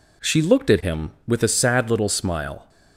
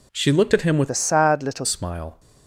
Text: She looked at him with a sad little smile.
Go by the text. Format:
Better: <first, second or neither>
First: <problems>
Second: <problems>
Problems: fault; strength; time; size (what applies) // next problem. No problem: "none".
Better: first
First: none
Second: changes voice from "a" to "little"; from 0.9 to 1.6 s; 0.7 s long